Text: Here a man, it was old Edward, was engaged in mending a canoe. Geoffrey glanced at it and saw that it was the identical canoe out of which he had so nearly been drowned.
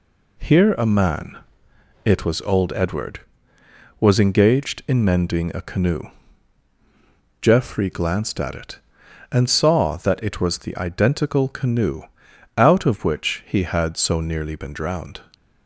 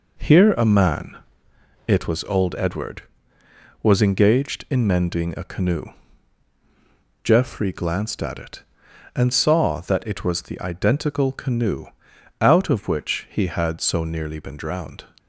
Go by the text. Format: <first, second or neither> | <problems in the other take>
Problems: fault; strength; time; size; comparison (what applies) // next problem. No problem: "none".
first | starts louder than the rest; noticeable; until 1.1 s; 4.5 dB // pauses between "canoe" and "out"; noticeable; at 11.8 s; 0.54 s long; noticeable in the first